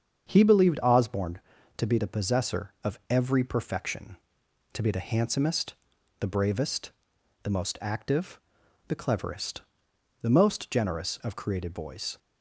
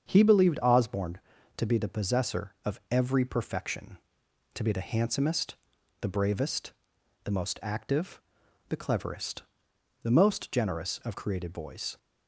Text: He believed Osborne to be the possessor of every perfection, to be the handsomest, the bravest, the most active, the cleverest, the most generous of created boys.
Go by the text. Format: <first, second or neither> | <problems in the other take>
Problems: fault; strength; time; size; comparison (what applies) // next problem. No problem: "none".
neither | starts louder than the rest; strong; the same in both